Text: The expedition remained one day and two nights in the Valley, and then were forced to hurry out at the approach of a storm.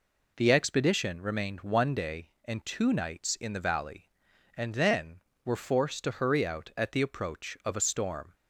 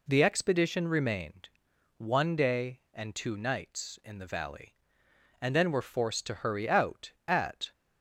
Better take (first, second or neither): first